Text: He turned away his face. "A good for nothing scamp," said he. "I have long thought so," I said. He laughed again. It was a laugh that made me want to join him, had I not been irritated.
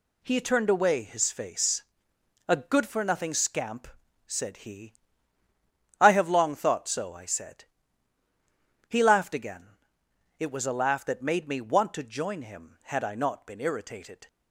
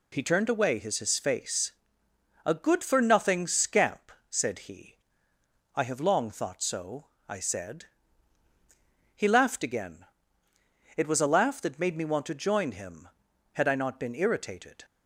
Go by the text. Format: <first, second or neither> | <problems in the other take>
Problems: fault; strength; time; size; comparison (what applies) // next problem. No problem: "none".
first | says "his" twice; at 0.9 s